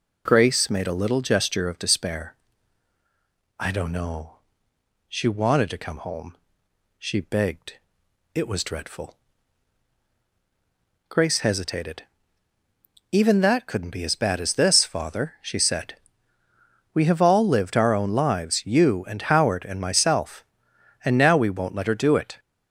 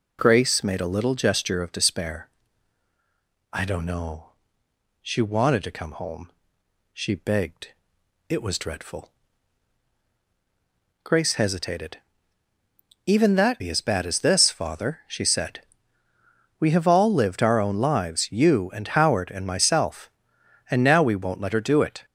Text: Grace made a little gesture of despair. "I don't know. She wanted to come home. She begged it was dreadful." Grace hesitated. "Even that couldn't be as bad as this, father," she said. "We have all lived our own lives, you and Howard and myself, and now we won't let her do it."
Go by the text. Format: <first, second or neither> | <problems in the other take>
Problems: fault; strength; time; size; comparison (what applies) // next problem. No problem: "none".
first | pauses between "begged" and "it"; noticeable; at 7.7 s; 0.56 s long; noticeable in the first // skips "couldn't"; at 13.6 s